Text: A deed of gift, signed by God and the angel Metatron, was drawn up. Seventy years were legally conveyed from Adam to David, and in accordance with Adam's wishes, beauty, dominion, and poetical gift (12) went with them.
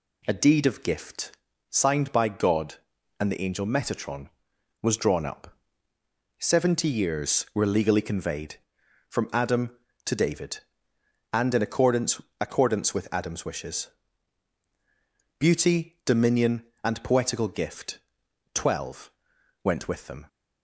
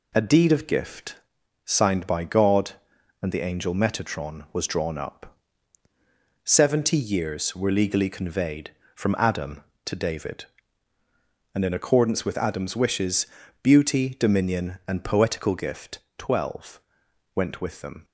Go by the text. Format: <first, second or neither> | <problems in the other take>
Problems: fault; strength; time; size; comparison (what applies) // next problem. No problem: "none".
second | says "accordance" twice; at 12.3 s